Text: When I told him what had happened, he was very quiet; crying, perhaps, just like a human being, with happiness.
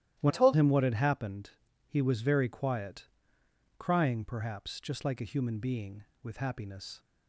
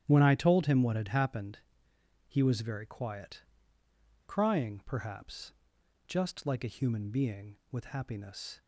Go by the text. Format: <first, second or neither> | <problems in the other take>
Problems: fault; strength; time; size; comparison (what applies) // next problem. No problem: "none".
second | starts louder than the rest; strong; until 1.2 s; 13 dB; strong in the second // changes voice from "I" to "told"; from 0.2 to 0.5 s; 0.3 s long